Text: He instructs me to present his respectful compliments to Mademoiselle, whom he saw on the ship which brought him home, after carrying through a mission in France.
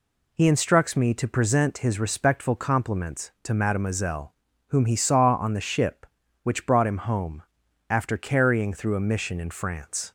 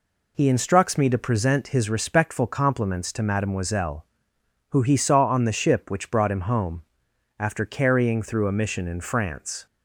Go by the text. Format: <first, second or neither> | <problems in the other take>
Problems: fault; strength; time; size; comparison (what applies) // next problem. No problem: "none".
first | says "who" for "whom"; at 4.7 s